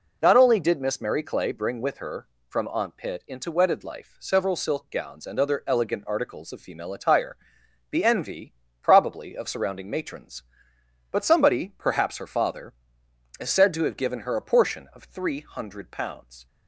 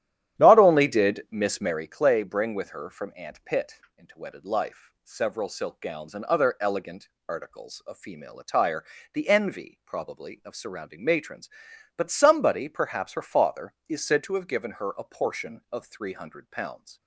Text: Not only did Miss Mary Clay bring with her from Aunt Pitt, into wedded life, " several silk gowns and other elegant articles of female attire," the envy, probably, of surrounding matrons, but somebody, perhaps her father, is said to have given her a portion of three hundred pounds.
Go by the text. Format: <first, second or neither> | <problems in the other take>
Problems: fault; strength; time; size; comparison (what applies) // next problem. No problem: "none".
first | starts louder than the rest; strong; until 1.8 s; 10.5 dB // pauses between "elegant" and "articles"; slight; at 7.0 s; 0.18 s long